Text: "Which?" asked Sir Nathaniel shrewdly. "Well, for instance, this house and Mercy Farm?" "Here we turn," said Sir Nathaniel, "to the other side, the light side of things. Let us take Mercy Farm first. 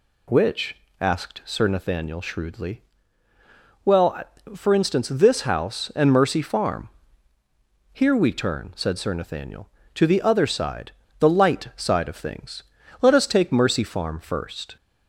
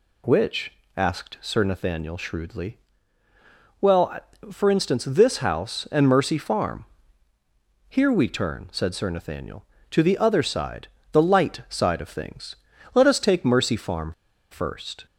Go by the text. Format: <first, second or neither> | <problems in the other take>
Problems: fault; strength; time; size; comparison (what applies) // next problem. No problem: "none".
first | pauses between "Farm" and "first"; at 14.1 s; 0.38 s long